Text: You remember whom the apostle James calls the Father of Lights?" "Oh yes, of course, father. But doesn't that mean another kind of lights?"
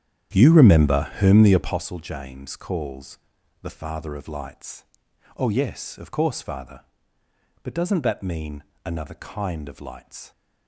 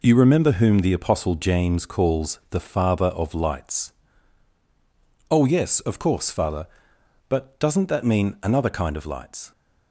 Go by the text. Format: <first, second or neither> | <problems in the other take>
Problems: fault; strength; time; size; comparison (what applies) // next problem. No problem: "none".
second | starts louder than the rest; strong; until 1.9 s; 10 dB // pauses between "calls" and "the"; at 3.1 s; 0.44 s long // pauses between "mean" and "another"; slight; at 8.6 s; 0.22 s long